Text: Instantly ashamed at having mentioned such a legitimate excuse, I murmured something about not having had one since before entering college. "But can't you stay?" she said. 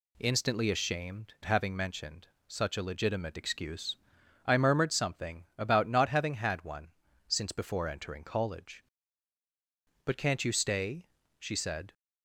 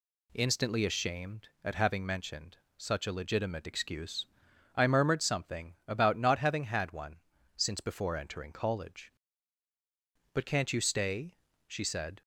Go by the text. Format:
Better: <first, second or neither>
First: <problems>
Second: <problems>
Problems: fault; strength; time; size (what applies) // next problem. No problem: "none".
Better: second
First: skips "at"; at 1.3 s // pauses between "mentioned" and "such"; slight; at 2.2 s; 0.20 s long // pauses between "one" and "since"; at 6.8 s; 0.38 s long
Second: pauses between "mentioned" and "such"; slight; at 2.5 s; 0.20 s long // pauses between "one" and "since"; at 7.1 s; 0.38 s long